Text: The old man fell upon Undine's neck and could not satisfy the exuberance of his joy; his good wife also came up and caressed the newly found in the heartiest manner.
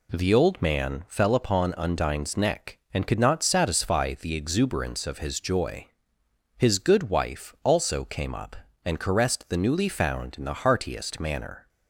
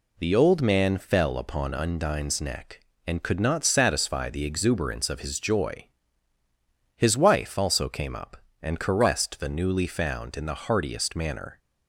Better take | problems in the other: first | skips "good"; at 7.1 s

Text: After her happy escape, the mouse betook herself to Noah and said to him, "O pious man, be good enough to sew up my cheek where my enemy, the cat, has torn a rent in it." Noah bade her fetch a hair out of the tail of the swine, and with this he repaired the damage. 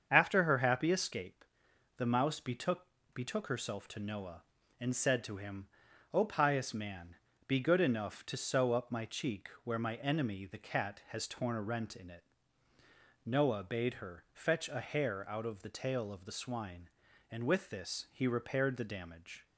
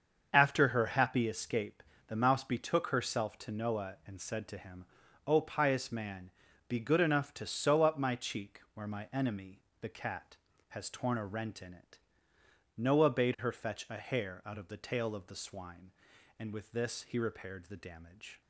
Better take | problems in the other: second | starts louder than the rest; strong; until 1.1 s; 7 dB; also in the second // says "betook" twice; at 3.1 s // pauses between "cheek" and "where"; slight; at 9.4 s; 0.16 s long

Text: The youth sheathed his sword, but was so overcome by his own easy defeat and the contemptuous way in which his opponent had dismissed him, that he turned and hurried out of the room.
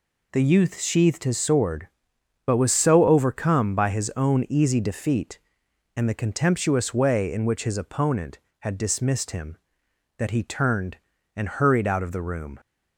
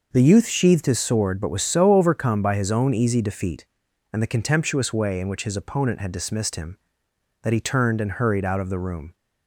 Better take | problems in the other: neither | none

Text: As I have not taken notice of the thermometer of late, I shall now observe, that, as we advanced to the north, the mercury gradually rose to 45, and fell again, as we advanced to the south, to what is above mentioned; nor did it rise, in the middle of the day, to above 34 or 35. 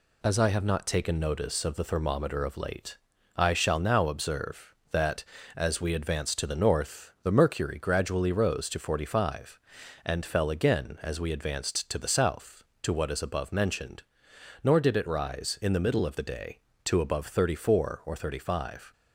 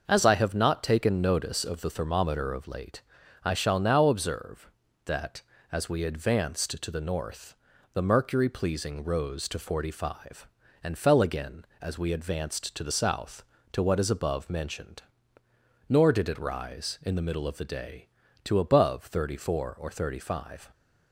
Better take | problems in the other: first | starts louder than the rest; noticeable; until 1.0 s; 6 dB // says "pleasing" for "gradually"; at 8.4 s

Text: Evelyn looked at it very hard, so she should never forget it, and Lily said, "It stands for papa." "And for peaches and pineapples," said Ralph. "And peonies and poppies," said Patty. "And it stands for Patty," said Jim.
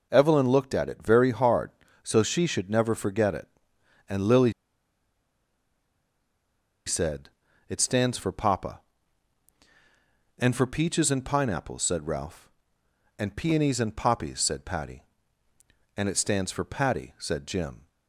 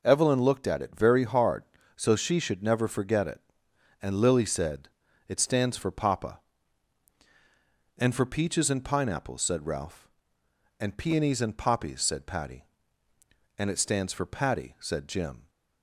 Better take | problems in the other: second | pauses between "Lily" and "said"; strong; at 4.5 s; 2.3 s long

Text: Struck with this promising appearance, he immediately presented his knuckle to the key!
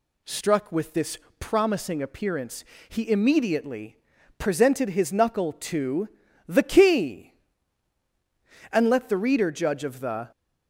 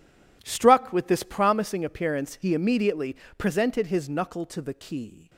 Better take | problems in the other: second | pauses between "this" and "promising"; slight; at 1.1 s; 0.22 s long // pauses between "immediately" and "presented"; at 3.9 s; 0.42 s long; slight in the second // pauses between "to" and "the"; at 6.0 s; 0.38 s long // goes on to say "And let the reader judge of the"; from 8.7 s on; 1.6 s long

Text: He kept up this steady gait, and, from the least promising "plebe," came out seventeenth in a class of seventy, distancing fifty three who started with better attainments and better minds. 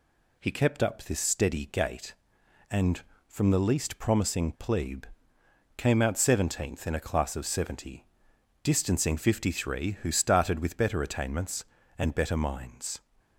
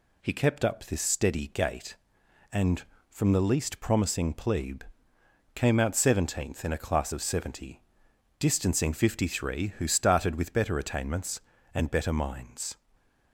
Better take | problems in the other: neither | none

